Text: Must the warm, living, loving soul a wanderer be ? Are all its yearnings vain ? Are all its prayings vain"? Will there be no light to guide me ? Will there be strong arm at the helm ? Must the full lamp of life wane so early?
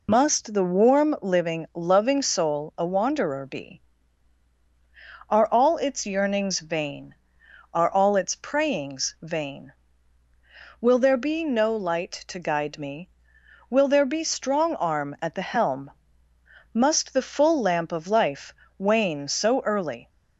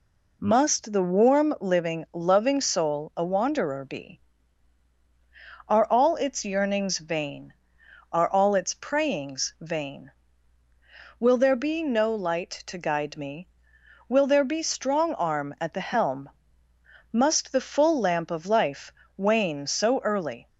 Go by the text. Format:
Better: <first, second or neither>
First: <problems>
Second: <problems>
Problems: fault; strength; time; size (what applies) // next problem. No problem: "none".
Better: second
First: loses the start of "Must"; at 0.0 s; 60 ms // pauses between "life" and "wane"; slight; at 18.5 s; 0.24 s long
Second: pauses between "life" and "wane"; slight; at 18.9 s; 0.24 s long